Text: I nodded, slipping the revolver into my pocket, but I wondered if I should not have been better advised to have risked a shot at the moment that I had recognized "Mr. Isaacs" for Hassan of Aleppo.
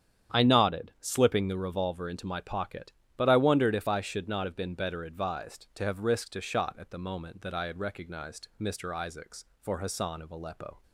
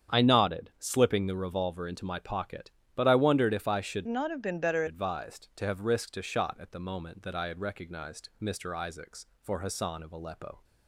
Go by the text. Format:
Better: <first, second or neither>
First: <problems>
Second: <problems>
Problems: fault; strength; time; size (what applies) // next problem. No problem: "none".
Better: first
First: starts louder than the rest; strong; until 1.4 s; 9 dB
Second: starts louder than the rest; strong; until 1.2 s; 8 dB // changes voice from "not" to "better"; from 4.0 to 4.8 s; 0.8 s long